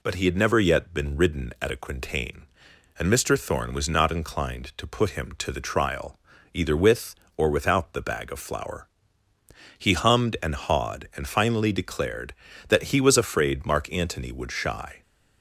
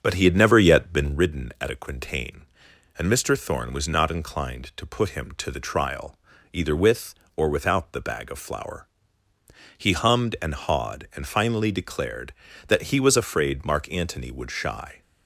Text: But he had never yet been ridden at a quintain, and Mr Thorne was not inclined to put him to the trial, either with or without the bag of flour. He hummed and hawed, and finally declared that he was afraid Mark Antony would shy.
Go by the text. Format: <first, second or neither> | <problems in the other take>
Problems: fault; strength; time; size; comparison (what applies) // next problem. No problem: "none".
first | starts louder than the rest; until 1.2 s; 7 dB